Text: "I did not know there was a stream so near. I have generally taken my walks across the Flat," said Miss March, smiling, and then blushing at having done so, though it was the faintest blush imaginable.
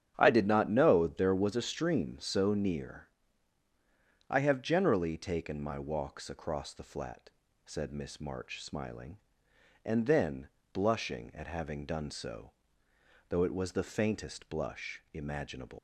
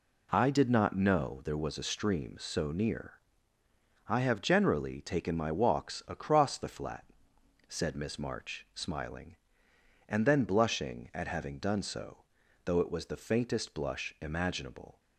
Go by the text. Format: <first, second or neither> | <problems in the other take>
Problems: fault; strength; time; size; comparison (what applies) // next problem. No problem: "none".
second | starts louder than the rest; strong; until 1.1 s; 9.5 dB // pauses between "then" and "blushing"; slight; at 10.4 s; 0.24 s long // leaves "imaginable" unfinished; at 15.7 s; 175 ms